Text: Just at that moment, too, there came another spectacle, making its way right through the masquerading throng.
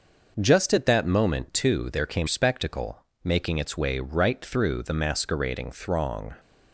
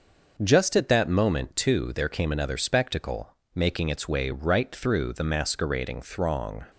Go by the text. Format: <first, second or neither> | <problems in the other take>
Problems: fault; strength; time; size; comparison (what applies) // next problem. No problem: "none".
second | skips "another"; at 2.2 s